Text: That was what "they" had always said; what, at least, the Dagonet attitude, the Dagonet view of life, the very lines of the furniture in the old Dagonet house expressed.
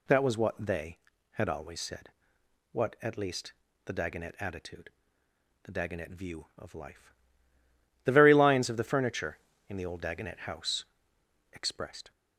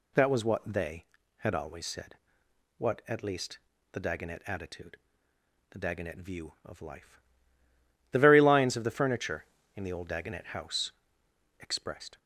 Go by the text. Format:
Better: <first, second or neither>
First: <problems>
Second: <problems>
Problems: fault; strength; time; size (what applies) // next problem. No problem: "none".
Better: neither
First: pauses between "house" and "expressed"; noticeable; at 10.8 s; 0.68 s long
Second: pauses between "house" and "expressed"; noticeable; at 10.9 s; 0.68 s long